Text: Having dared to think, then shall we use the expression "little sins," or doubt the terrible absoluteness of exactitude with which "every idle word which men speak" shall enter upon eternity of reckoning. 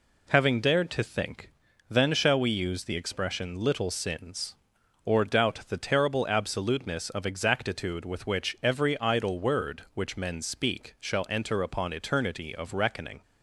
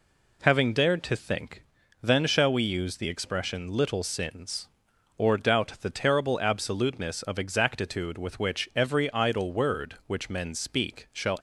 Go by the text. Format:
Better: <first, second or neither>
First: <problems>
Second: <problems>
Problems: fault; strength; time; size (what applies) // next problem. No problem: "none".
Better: first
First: none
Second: stops before "enter upon eternity of reckoning"; at 11.3 s